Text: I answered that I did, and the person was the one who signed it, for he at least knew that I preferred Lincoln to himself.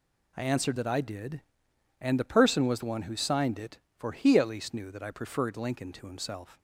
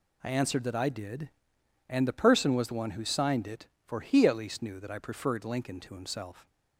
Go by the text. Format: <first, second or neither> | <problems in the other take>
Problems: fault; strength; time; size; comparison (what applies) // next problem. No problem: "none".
neither | none